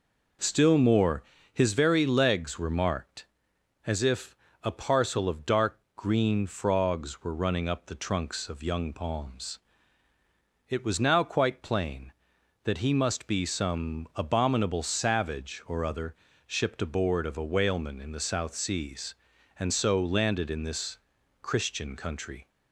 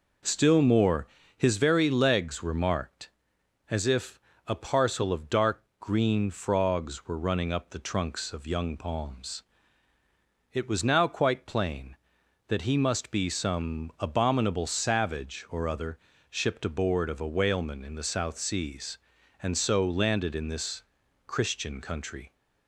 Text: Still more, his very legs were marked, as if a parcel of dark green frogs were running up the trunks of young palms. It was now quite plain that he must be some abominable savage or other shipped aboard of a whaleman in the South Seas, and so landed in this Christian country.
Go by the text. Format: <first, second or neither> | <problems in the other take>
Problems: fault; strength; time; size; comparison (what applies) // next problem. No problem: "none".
neither | pauses between "if" and "a"; slight; the same in both // pauses between "dark" and "green"; slight; the same in both // pauses between "other" and "shipped"; slight; the same in both // pauses between "this" and "Christian"; the same in both